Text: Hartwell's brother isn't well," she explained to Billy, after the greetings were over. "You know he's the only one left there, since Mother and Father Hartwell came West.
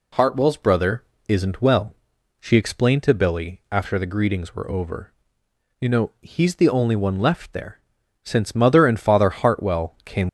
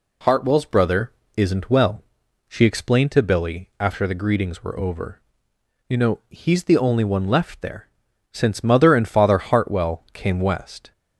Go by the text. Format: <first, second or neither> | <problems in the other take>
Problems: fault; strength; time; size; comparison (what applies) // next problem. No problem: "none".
second | pauses between "brother" and "isn't"; slight; at 1.0 s; 0.26 s long; slight in the second // stops before "West"; at 10.2 s